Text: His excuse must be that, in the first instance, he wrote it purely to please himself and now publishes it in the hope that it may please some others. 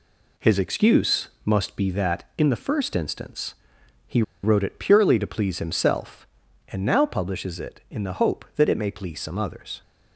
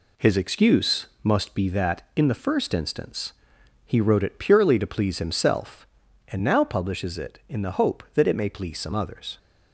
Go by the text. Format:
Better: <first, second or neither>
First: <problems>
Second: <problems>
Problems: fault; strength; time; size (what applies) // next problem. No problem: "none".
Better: second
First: pauses between "excuse" and "must"; slight; at 1.2 s; 0.16 s long // pauses between "he" and "wrote"; slight; at 4.2 s; 0.20 s long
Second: pauses between "excuse" and "must"; slight; at 1.0 s; 0.16 s long